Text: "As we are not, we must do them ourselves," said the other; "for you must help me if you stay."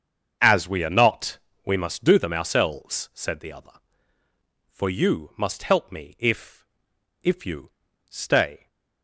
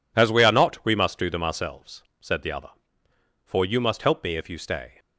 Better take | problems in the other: second | starts louder than the rest; until 1.6 s; 6.5 dB // says "if" twice; at 7.2 s // pauses between "you" and "stay"; at 7.7 s; 0.40 s long

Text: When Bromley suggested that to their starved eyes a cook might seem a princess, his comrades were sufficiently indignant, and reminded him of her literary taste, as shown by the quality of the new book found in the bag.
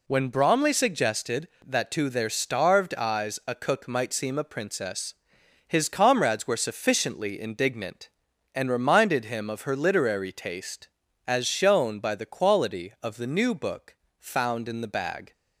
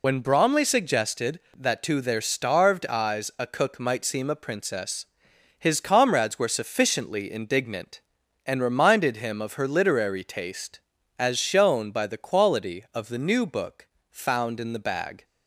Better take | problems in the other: first | loses the start of "When"; at 0.0 s; 50 ms // pauses between "book" and "found"; slight; at 13.8 s; 0.24 s long; slight in the first

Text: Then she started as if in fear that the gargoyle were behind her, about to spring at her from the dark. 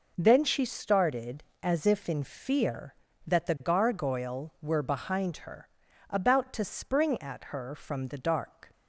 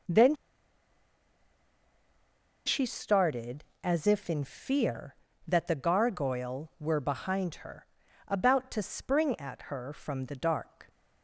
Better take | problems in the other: first | pauses between "Then" and "she"; strong; at 0.3 s; 2.3 s long

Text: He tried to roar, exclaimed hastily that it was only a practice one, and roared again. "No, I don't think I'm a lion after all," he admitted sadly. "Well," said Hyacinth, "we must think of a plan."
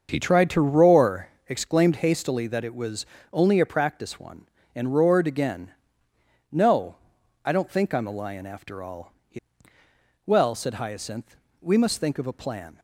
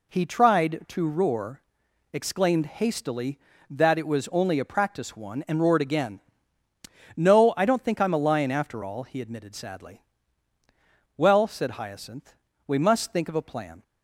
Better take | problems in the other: second | starts louder than the rest; until 1.1 s; 6.5 dB // pauses between "was" and "only"; slight; at 3.0 s; 0.26 s long // skips "admitted sadly"; at 9.8 s

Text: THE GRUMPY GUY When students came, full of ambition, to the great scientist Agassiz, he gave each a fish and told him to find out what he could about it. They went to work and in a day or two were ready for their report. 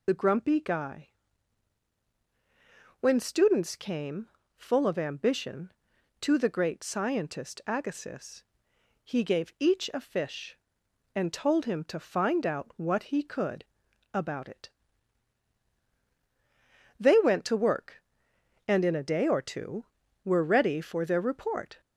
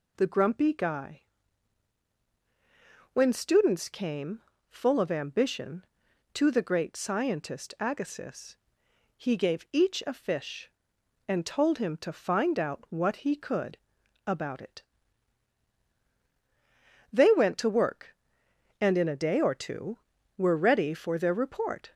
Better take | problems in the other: second | loses the start of "THE"; at 0.0 s; 40 ms // pauses between "GUY" and "When"; strong; at 1.0 s; 1.9 s long; strong in the second // pauses between "could" and "about"; noticeable; at 13.6 s; 0.50 s long; noticeable in the second

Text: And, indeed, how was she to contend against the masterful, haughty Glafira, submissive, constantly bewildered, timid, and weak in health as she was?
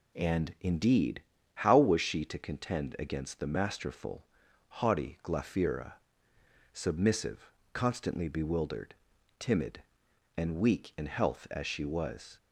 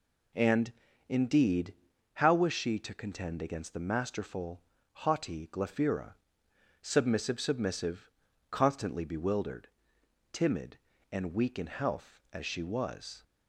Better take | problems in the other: first | says "submissive" twice; at 7.3 s

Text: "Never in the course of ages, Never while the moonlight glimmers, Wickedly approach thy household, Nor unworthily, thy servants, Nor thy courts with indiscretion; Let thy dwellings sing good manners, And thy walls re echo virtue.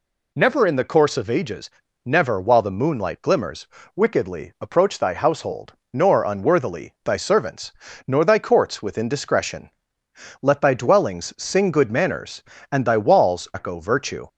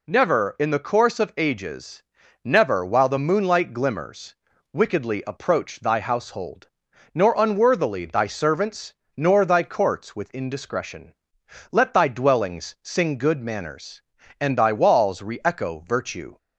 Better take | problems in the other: second | skips "re"; at 13.5 s

